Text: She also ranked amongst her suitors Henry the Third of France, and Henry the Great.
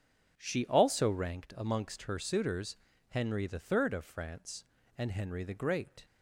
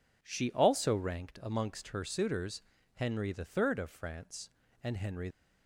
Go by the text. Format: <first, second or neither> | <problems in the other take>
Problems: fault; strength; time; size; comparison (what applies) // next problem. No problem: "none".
first | pauses between "suitors" and "Henry"; slight; at 2.6 s; 0.32 s long; slight in the first // stops before "the Great"; at 5.3 s